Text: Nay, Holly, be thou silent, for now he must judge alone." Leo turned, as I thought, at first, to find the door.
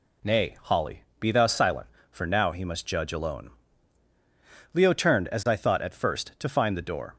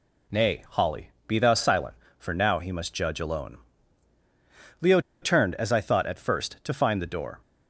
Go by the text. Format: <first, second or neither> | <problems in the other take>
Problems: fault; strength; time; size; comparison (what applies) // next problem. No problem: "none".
first | pauses between "Leo" and "turned"; slight; at 4.9 s; 0.22 s long